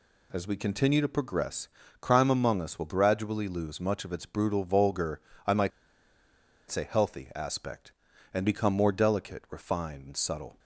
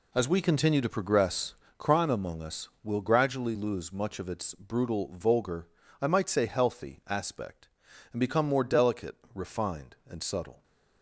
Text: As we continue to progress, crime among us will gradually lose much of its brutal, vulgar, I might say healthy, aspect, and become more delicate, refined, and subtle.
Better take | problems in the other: second | pauses between "might" and "say"; at 5.7 s; 1.0 s long

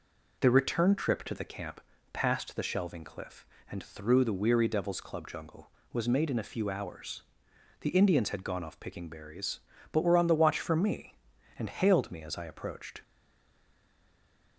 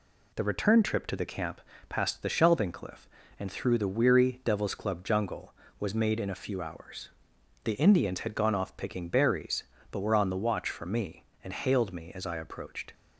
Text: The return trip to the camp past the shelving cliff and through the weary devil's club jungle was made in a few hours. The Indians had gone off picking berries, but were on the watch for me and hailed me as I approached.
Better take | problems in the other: second | pauses between "camp" and "past"; slight; at 1.7 s; 0.32 s long; slight in the second // stays silent after the last word; noticeable; from 13.0 s on; 1.5 s long

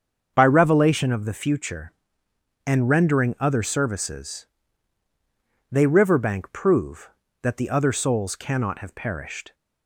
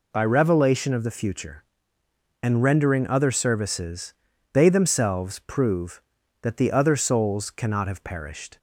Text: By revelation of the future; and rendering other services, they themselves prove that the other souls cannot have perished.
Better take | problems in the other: second | starts louder than the rest; until 1.3 s; 7 dB // says "riverbank" for "themselves"; at 5.8 s

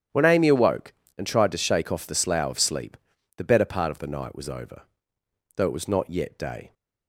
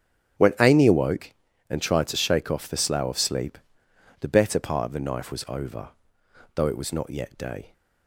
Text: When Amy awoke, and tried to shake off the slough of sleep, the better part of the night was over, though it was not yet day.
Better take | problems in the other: first | starts louder than the rest; strong; until 1.7 s; 10 dB; strong in the first // says "knife" for "night"; at 4.9 s

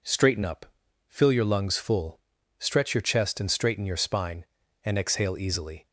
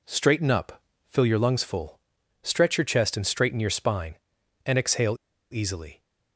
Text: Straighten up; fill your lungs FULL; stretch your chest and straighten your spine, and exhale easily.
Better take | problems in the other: first | pauses between "exhale" and "easily"; slight; at 5.1 s; 0.35 s long

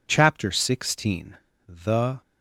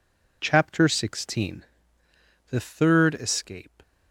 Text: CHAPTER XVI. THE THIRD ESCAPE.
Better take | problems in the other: second | stops before "THIRD ESCAPE"; at 2.2 s

